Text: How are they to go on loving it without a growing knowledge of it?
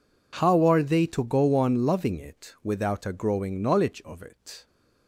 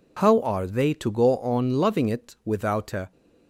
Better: first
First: none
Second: stops before "growing knowledge of it"; at 3.1 s

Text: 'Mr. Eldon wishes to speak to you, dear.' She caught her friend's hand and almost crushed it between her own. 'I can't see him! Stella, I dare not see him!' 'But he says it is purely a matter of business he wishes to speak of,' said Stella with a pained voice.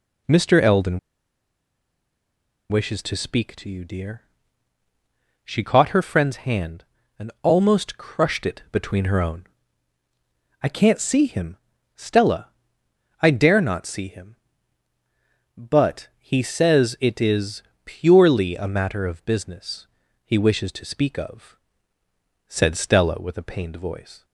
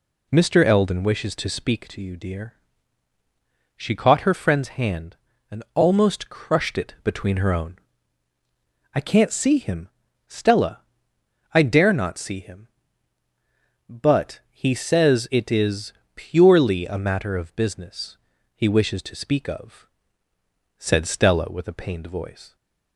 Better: second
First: pauses between "Eldon" and "wishes"; strong; at 0.9 s; 1.7 s long // pauses between "is" and "purely"; slight; at 17.6 s; 0.22 s long // pauses between "business" and "he"; at 19.8 s; 0.38 s long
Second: pauses between "is" and "purely"; slight; at 15.9 s; 0.22 s long // pauses between "business" and "he"; at 18.1 s; 0.38 s long

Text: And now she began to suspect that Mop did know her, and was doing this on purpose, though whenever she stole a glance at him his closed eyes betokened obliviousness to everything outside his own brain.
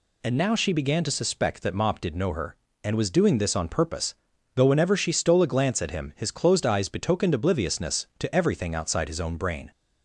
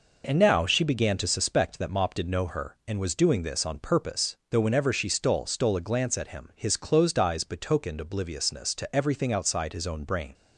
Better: first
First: none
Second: says "stole" twice; at 5.4 s

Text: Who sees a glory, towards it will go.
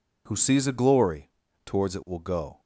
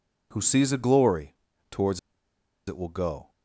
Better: first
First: none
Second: pauses between "towards" and "it"; noticeable; at 1.9 s; 0.68 s long

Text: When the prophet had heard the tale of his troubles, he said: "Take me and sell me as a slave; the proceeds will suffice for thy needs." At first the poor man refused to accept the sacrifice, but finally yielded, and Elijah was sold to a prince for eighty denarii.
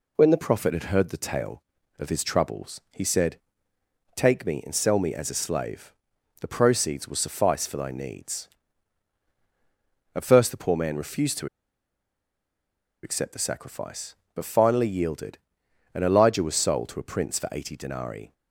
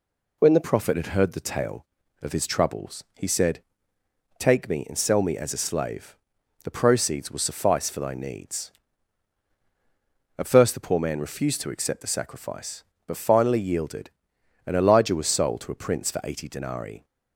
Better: second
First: pauses between "to" and "accept"; strong; at 11.4 s; 1.5 s long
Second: none

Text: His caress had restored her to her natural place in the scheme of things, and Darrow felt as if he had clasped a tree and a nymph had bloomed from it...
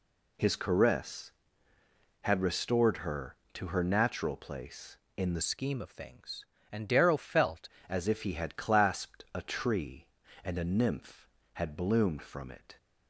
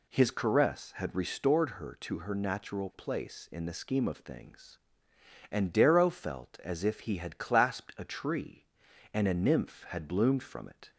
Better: second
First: changes voice from "scheme" to "felt"; from 5.4 to 7.6 s; 2.2 s long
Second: none

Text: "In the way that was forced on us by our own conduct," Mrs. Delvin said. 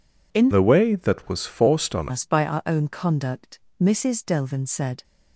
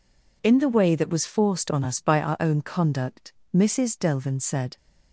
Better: second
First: changes voice from "the" to "on"; from 0.5 to 2.0 s; 1.5 s long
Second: none

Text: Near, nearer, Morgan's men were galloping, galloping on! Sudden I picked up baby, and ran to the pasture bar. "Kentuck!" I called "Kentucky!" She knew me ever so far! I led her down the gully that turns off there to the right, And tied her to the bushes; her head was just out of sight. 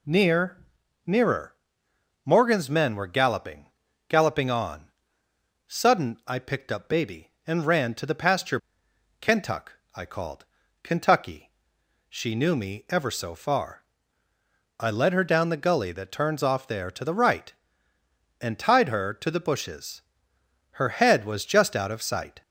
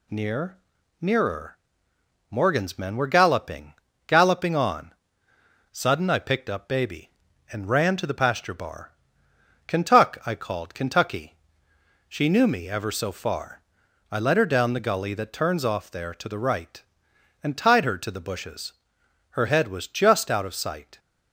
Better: second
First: skips "bar"; at 8.8 s // pauses between "called" and "Kentucky"; at 10.4 s; 0.38 s long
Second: none

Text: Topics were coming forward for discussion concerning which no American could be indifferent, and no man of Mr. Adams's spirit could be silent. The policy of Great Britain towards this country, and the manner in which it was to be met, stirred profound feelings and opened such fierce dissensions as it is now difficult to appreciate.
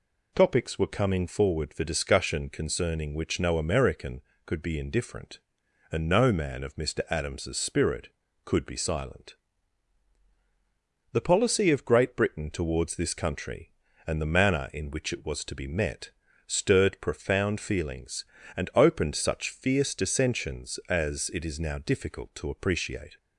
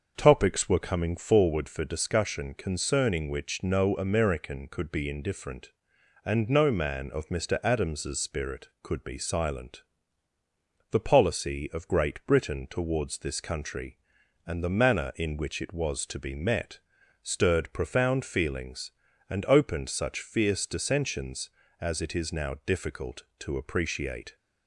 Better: first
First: none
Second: starts louder than the rest; until 1.6 s; 6.5 dB

